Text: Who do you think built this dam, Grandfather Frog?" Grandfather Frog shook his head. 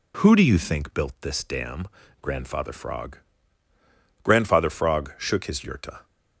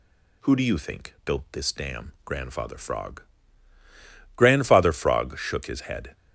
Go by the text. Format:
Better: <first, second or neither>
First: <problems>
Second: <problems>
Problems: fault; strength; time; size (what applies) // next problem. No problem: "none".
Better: second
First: says "yurta" for "head"; at 5.5 s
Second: none